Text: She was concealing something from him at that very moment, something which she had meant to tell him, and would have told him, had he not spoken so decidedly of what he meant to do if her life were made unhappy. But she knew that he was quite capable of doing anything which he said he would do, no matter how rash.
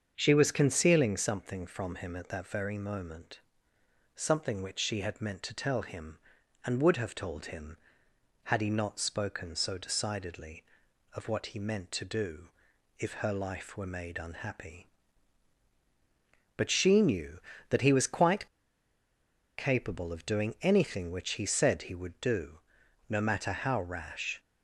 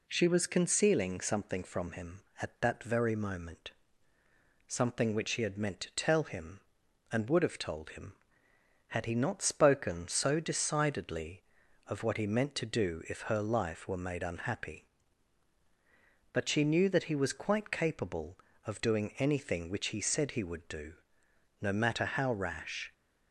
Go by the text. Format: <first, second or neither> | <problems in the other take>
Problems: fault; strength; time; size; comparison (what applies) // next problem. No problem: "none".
second | starts louder than the rest; until 1.1 s; 7 dB // pauses between "do" and "if"; noticeable; at 12.4 s; 0.50 s long // pauses between "quite" and "capable"; at 18.4 s; 1.1 s long